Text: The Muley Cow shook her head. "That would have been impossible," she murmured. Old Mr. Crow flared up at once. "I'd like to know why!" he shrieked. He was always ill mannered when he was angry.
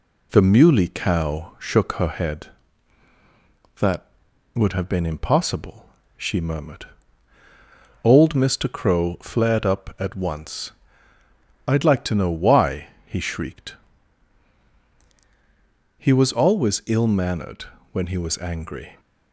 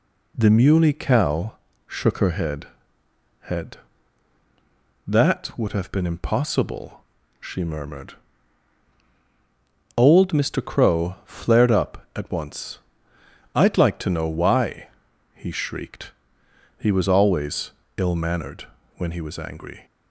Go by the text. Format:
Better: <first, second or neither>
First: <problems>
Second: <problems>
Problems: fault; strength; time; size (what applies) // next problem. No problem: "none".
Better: first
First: pauses between "mannered" and "when"; slight; at 17.6 s; 0.28 s long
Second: pauses between "Cow" and "shook"; slight; at 1.5 s; 0.34 s long // says "head" twice; at 3.4 s // pauses between "always" and "ill"; slight; at 17.7 s; 0.24 s long // pauses between "mannered" and "when"; slight; at 18.6 s; 0.32 s long